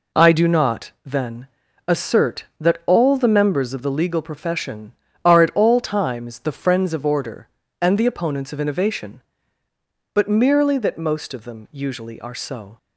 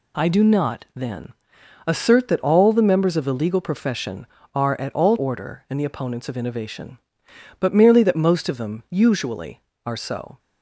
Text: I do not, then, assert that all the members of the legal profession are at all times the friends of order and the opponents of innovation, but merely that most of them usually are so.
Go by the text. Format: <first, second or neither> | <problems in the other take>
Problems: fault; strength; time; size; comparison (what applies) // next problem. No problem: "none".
first | skips "times the friends of"; at 5.1 s